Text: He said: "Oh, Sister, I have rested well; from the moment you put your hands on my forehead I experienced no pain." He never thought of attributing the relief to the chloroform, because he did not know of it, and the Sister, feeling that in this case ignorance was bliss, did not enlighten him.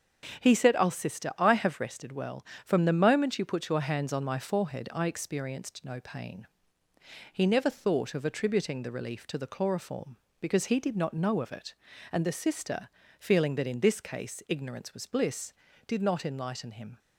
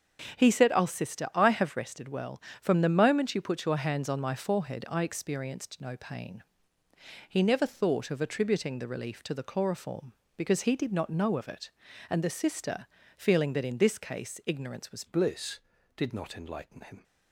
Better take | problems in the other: first | starts louder than the rest; strong; until 1.4 s; 8.5 dB; strong in the first // changes voice at "bliss"; from 15.0 s on; 2.0 s long

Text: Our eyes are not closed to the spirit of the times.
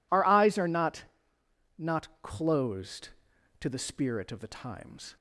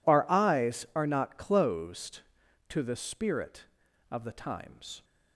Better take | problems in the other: second | says "not" twice; at 1.7 s

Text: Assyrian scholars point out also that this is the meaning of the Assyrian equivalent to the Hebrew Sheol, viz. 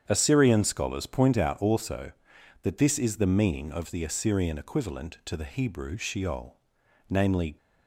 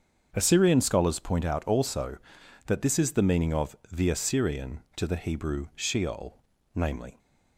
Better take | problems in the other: first | starts louder than the rest; until 1.3 s; 7 dB; strong in the first // skips "equivalent"; at 4.8 s

